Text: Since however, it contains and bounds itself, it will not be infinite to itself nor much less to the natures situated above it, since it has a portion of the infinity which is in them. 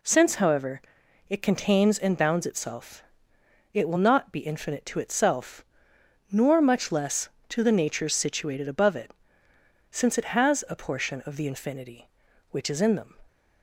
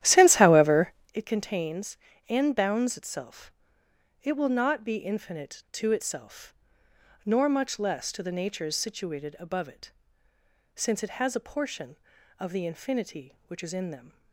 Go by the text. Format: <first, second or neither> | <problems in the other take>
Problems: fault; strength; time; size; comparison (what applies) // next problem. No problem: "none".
first | starts louder than the rest; strong; until 1.2 s; 12 dB // pauses between "itself" and "nor"; noticeable; at 6.5 s; 0.72 s long; noticeable in the first